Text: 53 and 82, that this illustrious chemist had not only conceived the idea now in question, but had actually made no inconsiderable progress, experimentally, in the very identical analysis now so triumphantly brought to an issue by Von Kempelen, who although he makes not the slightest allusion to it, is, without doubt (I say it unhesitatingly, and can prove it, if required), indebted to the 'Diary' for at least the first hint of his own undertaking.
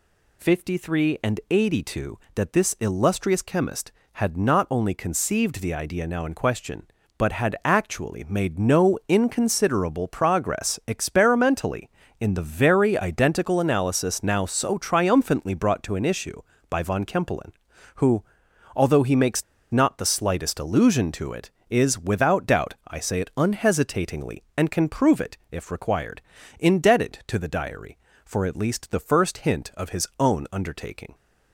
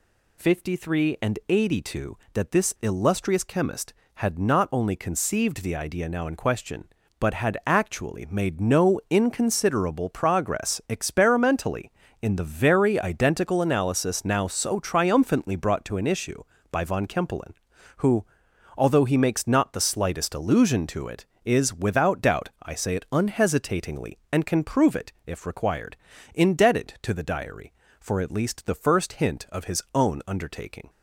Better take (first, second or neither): second